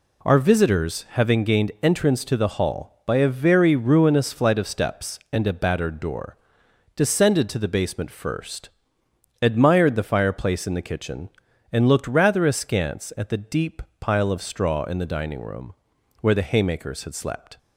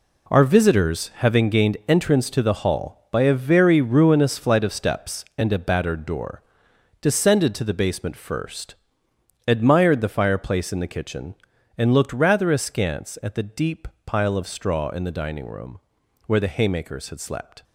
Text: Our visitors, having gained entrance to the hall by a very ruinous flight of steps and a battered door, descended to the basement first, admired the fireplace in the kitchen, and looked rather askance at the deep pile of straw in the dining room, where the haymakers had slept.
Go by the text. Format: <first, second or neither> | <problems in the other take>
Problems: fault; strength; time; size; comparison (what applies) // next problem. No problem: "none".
first | gets quieter; strong; throughout; 9.5 dB // pauses between "deep" and "pile"; slight; at 13.8 s; 0.18 s long; slight in the first